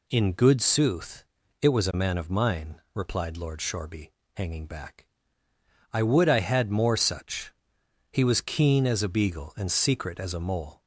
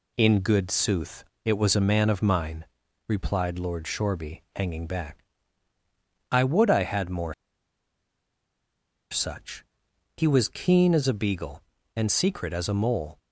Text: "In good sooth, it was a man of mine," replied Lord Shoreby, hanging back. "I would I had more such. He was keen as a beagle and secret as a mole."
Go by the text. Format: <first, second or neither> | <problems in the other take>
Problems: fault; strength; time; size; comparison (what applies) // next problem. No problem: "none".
first | pauses between "more" and "such"; strong; at 7.3 s; 1.7 s long